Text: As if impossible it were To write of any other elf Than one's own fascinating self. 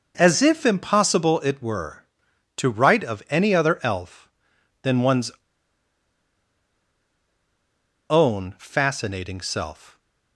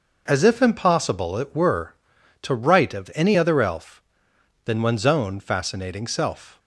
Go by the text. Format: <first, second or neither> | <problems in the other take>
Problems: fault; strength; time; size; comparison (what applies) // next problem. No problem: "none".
second | pauses between "one's" and "own"; strong; at 5.2 s; 2.7 s long